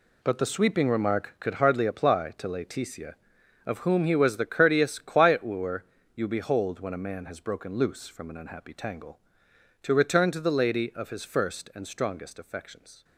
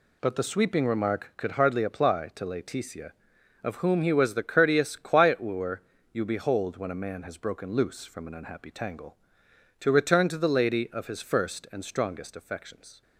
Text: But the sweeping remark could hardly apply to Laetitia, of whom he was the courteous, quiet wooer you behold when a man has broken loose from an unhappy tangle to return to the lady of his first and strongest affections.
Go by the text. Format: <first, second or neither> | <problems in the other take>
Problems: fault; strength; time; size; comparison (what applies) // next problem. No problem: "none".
second | gets quieter; strong; throughout; 11 dB // pauses between "wooer" and "you"; slight; at 5.8 s; 0.30 s long; slight in the second